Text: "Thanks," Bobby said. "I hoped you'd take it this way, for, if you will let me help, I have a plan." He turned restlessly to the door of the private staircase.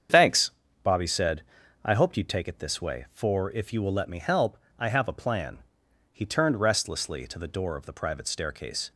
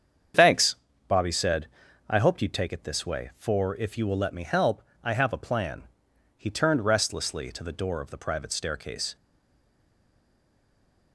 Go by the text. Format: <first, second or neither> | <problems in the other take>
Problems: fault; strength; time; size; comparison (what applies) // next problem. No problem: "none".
first | starts louder than the rest; strong; until 2.1 s; 7.5 dB; strong in the first // stays silent after the last word; noticeable; from 9.1 s on; 2.0 s long